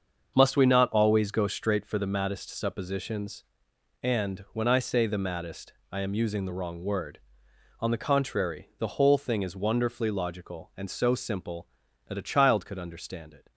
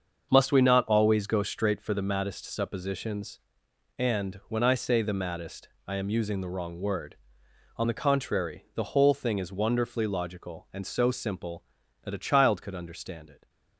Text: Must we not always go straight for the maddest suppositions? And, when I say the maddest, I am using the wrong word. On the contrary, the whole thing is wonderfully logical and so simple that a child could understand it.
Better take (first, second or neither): neither